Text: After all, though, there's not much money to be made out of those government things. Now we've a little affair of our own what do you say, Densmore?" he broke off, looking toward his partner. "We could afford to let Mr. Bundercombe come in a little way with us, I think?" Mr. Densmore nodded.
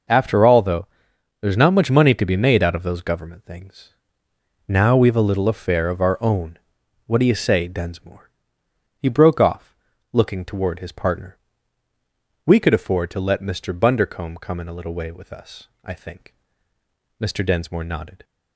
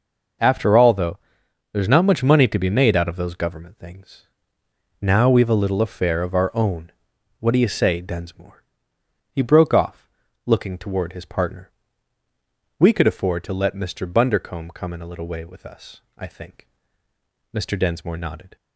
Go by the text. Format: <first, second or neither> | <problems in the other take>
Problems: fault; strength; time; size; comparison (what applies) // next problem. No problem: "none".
neither | pauses between "own" and "what"; noticeable; the same in both